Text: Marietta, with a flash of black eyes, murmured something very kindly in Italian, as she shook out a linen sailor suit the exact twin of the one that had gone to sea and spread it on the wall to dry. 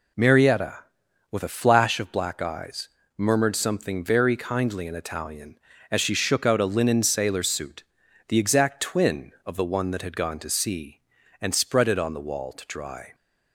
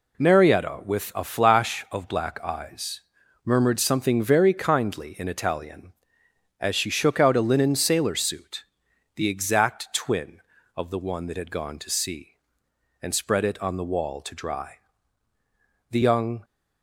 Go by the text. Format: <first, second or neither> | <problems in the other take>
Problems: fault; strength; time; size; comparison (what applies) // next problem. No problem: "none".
first | pauses between "suit" and "the"; noticeable; at 8.6 s; 0.54 s long; also in the first // goes on to say "The young"; from 15.9 s on; 0.53 s long